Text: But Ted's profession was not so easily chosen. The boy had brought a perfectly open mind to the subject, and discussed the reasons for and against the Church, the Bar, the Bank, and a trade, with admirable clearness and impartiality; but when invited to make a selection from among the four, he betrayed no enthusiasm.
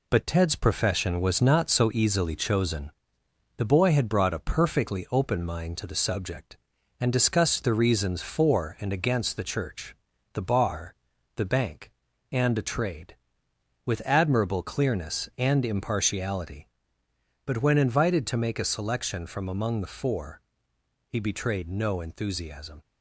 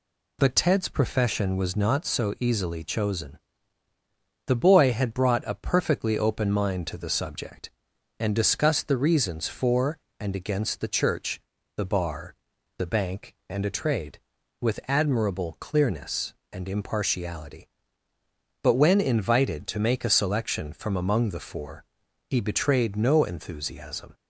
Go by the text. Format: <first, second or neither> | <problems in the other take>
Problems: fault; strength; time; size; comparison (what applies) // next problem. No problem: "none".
second | gets quieter; noticeable; throughout; 4.5 dB